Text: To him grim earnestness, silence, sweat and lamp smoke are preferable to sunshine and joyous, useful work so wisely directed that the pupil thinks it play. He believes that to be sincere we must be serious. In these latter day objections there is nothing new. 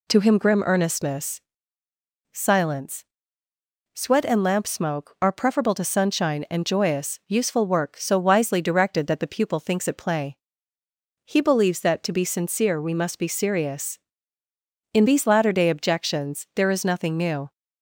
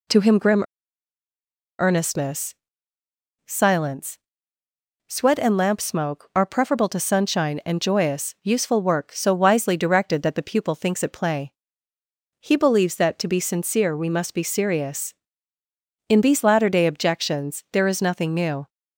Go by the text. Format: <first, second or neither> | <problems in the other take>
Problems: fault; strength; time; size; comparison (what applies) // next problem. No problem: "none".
first | pauses between "grim" and "earnestness"; at 0.6 s; 1.1 s long